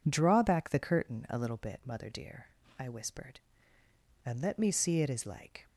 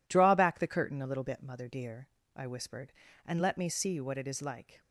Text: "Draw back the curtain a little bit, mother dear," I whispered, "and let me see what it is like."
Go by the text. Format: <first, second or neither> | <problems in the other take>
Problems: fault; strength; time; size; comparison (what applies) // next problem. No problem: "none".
second | skips "what"; at 5.0 s